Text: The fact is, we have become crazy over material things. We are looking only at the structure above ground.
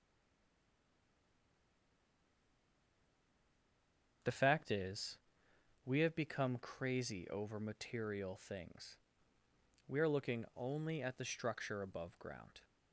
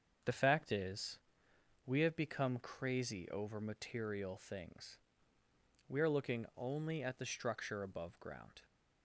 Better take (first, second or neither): second